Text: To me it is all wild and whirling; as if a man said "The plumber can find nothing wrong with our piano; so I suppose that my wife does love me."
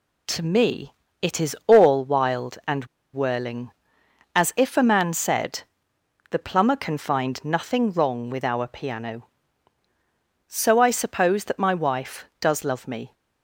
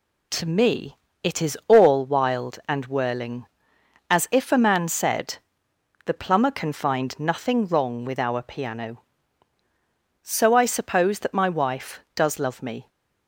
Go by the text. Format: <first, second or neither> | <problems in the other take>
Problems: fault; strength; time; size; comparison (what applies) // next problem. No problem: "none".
second | pauses between "me" and "it"; slight; at 0.9 s; 0.28 s long; slight in the second // pauses between "and" and "whirling"; slight; at 2.8 s; 0.28 s long // pauses between "said" and "The"; noticeable; at 5.6 s; 0.70 s long; noticeable in the second